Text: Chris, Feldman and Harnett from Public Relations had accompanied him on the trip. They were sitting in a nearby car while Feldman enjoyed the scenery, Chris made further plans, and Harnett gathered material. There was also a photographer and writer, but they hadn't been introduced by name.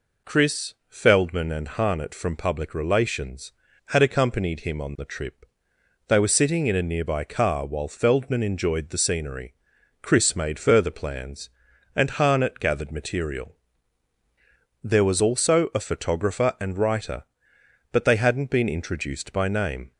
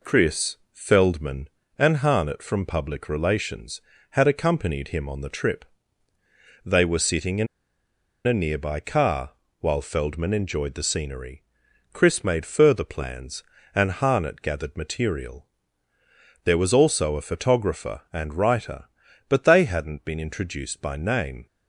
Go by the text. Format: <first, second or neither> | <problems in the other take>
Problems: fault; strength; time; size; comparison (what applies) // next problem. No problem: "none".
first | pauses between "in" and "a"; noticeable; at 7.4 s; 0.79 s long // pauses between "car" and "while"; slight; at 9.3 s; 0.28 s long